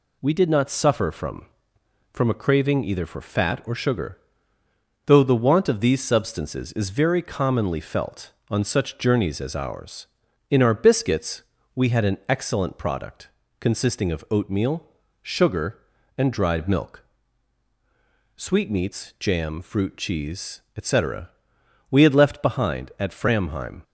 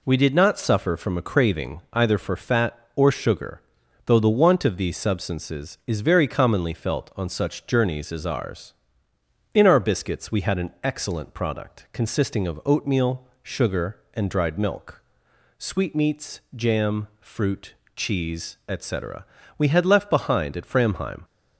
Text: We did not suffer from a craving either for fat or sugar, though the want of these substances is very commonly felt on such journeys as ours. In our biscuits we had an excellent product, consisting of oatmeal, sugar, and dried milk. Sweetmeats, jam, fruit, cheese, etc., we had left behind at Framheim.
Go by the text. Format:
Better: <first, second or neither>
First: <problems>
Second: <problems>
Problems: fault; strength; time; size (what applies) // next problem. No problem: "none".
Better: second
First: says "from" twice; at 2.1 s // pauses between "biscuits" and "we"; slight; at 11.4 s; 0.32 s long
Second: none